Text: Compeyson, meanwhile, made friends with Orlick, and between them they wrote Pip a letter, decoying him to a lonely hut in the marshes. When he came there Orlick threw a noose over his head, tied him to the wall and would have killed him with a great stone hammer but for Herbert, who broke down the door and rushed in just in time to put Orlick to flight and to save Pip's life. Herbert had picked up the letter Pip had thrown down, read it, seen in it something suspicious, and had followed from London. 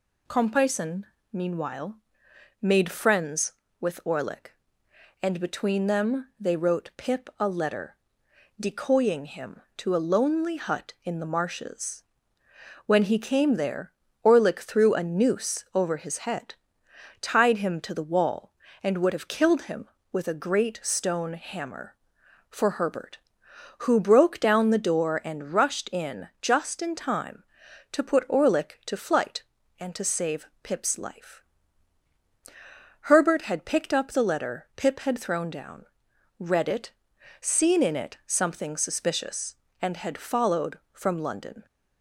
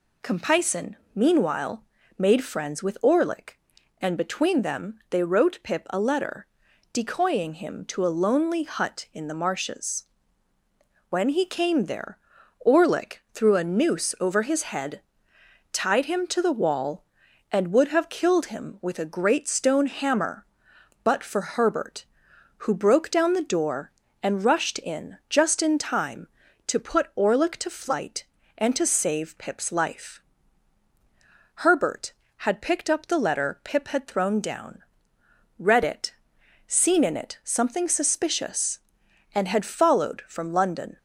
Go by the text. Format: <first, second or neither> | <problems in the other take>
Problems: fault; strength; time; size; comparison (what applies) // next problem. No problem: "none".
second | pauses between "there" and "Orlick"; slight; at 13.9 s; 0.32 s long; also in the second // skips "but"; at 22.2 s // pauses between "save" and "Pip's"; slight; at 30.4 s; 0.16 s long